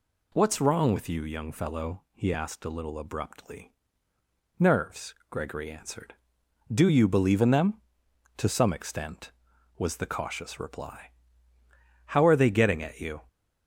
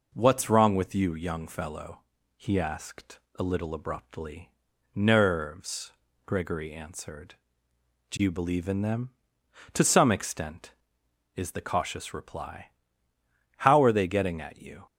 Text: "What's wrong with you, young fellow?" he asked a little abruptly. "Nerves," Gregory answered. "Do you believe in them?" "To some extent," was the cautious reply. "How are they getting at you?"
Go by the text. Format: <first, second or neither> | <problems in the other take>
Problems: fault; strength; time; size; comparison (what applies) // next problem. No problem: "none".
first | pauses between "asked" and "a"; slight; at 3.1 s; 0.20 s long // says "is" for "was"; at 11.3 s